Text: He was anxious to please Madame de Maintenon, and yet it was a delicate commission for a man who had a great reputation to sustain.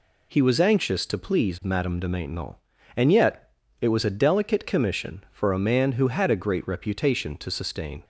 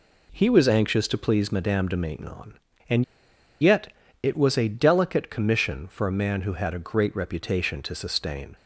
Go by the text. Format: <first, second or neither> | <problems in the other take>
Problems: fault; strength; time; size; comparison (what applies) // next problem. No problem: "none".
first | pauses between "and" and "yet"; noticeable; at 3.0 s; 0.56 s long // pauses between "yet" and "it"; slight; at 3.9 s; 0.32 s long; slight in the first